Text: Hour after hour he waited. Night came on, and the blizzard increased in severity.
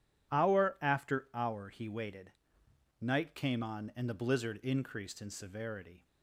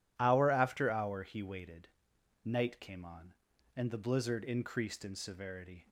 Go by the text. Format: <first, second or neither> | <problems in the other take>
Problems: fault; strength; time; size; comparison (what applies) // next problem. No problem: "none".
neither | none